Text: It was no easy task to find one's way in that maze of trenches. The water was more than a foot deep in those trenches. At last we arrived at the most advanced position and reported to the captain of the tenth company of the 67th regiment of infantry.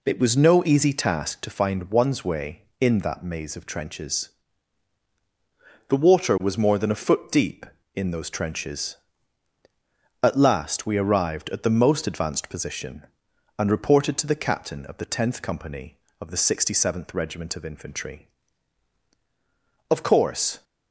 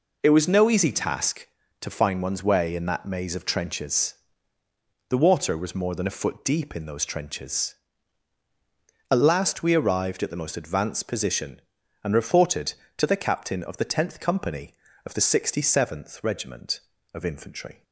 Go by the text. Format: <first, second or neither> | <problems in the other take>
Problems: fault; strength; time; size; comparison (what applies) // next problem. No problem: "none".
second | goes on to say "Of course"; noticeable; from 19.8 s on; 0.74 s long